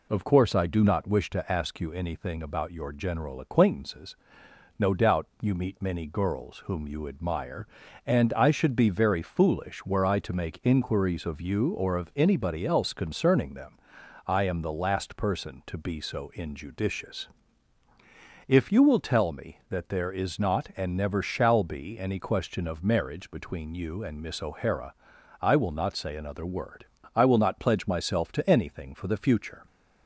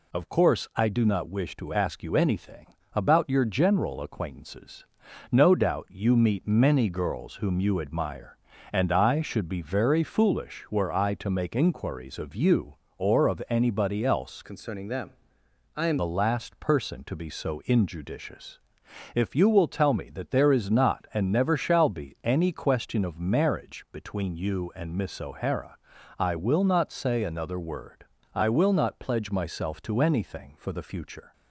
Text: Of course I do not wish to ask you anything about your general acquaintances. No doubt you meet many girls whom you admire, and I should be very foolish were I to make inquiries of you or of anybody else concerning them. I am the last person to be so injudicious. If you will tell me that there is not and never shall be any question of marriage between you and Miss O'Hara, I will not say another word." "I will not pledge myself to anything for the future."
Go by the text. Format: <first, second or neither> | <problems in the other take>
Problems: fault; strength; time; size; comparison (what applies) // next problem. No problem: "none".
first | pauses between "anything" and "about"; slight; at 2.6 s; 0.28 s long // changes voice from "concerning" to "am"; from 14.4 to 15.9 s; 1.5 s long